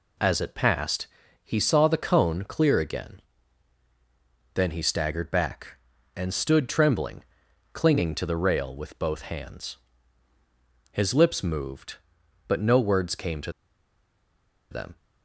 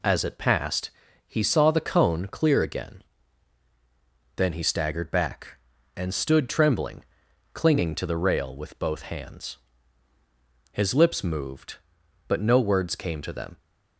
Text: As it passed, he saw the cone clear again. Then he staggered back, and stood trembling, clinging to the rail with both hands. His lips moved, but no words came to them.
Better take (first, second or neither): second